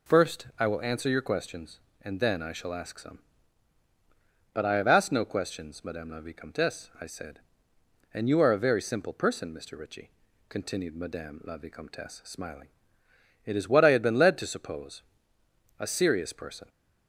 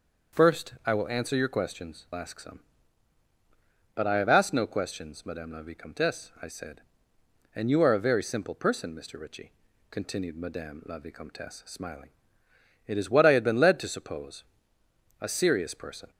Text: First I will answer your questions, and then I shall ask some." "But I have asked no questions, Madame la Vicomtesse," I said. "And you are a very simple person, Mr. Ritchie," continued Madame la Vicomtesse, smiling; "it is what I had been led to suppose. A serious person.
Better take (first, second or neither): first